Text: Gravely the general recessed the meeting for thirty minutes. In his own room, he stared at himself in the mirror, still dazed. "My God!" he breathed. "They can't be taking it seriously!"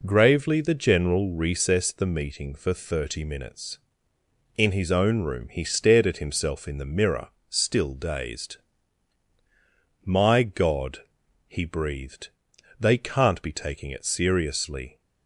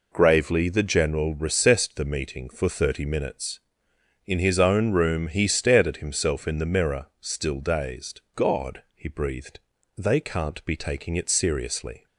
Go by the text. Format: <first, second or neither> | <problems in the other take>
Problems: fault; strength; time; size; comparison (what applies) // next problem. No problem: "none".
first | skips "My"; at 8.2 s